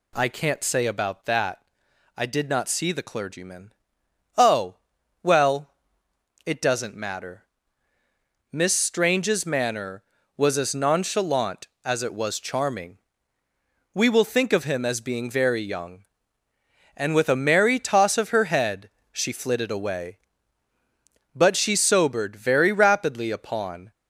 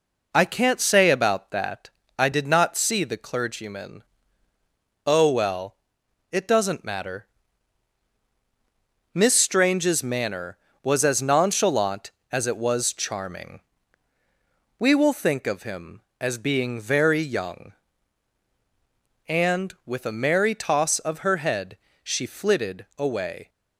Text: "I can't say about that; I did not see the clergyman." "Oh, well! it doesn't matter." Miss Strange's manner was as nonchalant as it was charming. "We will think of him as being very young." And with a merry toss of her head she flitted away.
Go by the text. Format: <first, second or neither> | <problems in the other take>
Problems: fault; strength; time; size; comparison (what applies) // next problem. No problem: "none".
second | pauses between "head" and "she"; slight; at 18.8 s; 0.22 s long; slight in the second // goes on to say "But she sobered very rapidly upon"; strong; from 21.3 s on; 2.5 s long